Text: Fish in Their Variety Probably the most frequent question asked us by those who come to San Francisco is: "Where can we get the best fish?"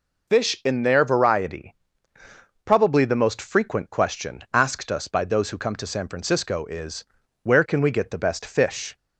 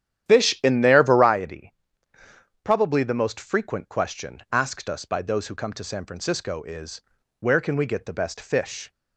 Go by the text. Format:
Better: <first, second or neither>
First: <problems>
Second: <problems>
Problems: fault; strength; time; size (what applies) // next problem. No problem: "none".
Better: first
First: pauses between "Variety" and "Probably"; noticeable; at 1.7 s; 0.92 s long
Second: starts louder than the rest; strong; until 1.4 s; 11 dB // pauses between "Variety" and "Probably"; noticeable; at 1.7 s; 0.92 s long